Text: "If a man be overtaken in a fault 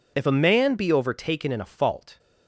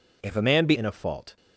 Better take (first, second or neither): first